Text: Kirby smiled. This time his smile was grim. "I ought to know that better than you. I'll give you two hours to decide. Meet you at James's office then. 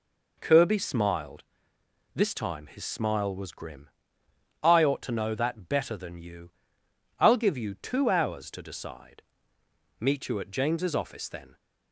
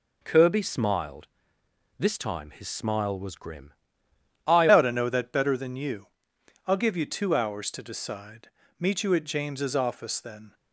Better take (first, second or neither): first